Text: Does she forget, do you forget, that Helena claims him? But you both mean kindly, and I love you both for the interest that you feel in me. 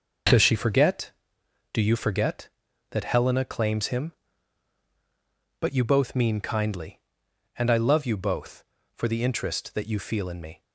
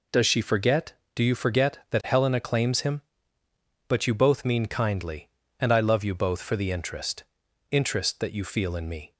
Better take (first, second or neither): first